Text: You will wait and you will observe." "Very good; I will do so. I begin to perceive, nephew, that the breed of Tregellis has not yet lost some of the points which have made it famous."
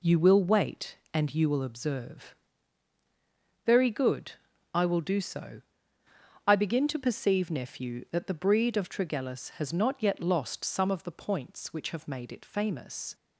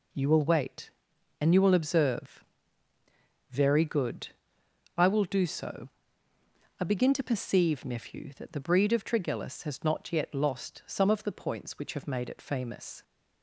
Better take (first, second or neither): neither